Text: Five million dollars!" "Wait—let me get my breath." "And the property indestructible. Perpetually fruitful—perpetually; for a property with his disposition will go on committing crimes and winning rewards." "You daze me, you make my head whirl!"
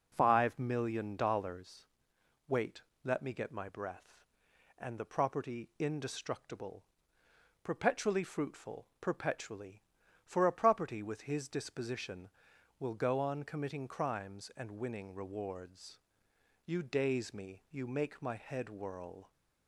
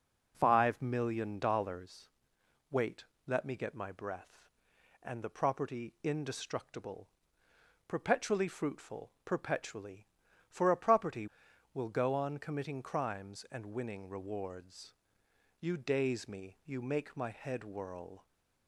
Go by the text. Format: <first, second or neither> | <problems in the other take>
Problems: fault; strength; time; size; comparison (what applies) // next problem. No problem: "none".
first | skips "with his disposition"; at 11.4 s